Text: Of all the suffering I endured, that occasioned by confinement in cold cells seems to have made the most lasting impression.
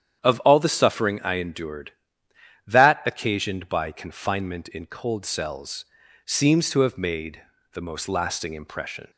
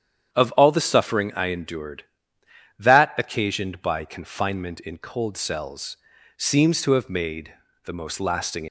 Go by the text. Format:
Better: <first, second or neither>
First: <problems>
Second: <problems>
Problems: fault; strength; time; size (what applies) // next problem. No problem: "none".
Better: first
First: starts louder than the rest; strong; until 1.2 s; 9 dB // pauses between "cells" and "seems"; at 5.8 s; 0.40 s long // pauses between "made" and "the"; slight; at 7.4 s; 0.32 s long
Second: starts louder than the rest; strong; until 1.3 s; 8.5 dB // pauses between "cells" and "seems"; at 5.9 s; 0.40 s long // pauses between "made" and "the"; slight; at 7.5 s; 0.32 s long // stops before "impression"; at 8.6 s